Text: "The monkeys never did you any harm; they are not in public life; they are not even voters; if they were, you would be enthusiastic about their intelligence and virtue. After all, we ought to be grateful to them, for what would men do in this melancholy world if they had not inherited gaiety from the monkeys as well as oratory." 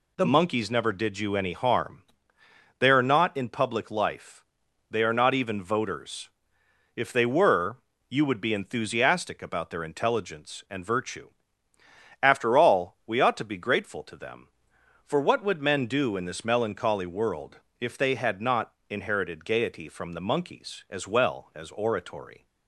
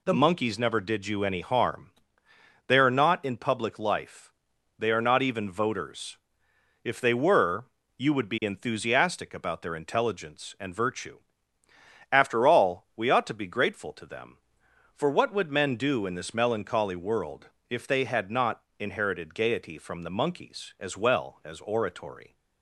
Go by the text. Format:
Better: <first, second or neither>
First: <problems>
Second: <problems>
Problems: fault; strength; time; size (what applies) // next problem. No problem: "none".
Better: neither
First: pauses between "world" and "if"; slight; at 17.5 s; 0.22 s long // pauses between "not" and "inherited"; slight; at 18.7 s; 0.20 s long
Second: pauses between "world" and "if"; slight; at 17.4 s; 0.22 s long // pauses between "not" and "inherited"; slight; at 18.6 s; 0.20 s long